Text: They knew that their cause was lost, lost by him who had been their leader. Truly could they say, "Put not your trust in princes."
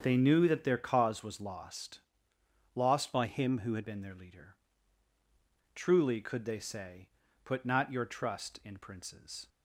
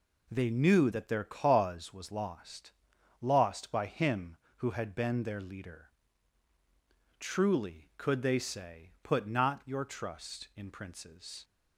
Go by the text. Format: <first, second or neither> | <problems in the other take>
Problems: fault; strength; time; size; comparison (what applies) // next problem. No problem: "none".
second | starts louder than the rest; until 1.0 s; 7 dB // changes voice from "by" to "had"; from 3.1 to 3.8 s; 0.7 s long